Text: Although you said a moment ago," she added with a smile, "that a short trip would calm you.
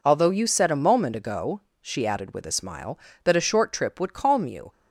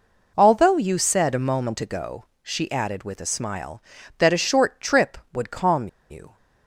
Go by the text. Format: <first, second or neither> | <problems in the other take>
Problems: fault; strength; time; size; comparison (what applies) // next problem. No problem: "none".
first | pauses between "calm" and "you"; slight; at 5.8 s; 0.22 s long